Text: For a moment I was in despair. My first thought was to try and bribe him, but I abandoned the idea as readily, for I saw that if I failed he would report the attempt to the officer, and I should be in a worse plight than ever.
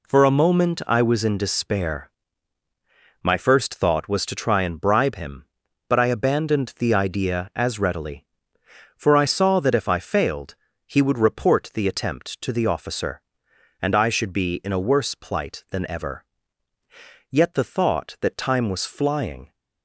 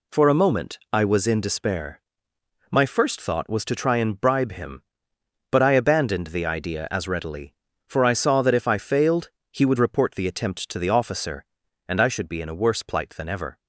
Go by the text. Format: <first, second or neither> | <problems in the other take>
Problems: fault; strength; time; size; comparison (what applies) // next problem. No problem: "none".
second | pauses between "failed" and "he"; slight; at 10.5 s; 0.30 s long; slight in the second // goes on to say "Yet the thought that time was flying"; strong; from 17.2 s on; 2.2 s long